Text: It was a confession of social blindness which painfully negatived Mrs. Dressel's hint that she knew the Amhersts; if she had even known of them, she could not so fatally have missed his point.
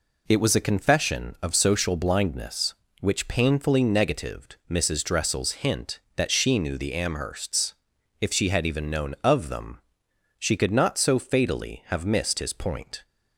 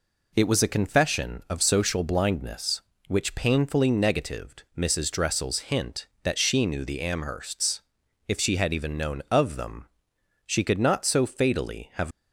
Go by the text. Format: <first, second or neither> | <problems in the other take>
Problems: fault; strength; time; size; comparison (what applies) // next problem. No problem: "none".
first | stops before "missed his point"; at 12.1 s